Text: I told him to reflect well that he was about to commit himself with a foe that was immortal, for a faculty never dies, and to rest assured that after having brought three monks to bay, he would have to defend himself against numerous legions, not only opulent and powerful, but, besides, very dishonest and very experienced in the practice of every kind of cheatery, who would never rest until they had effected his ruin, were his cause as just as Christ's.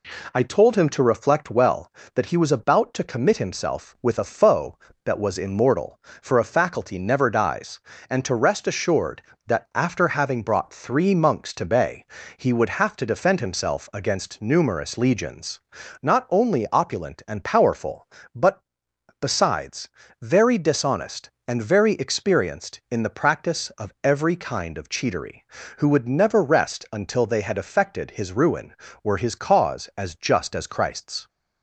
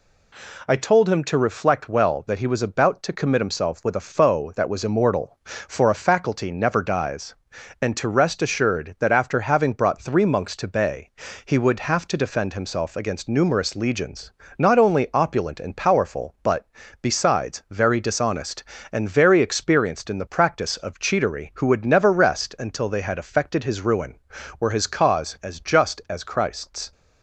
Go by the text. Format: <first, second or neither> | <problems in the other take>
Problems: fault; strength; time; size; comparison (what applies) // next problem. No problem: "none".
first | skips "of every kind"; at 20.7 s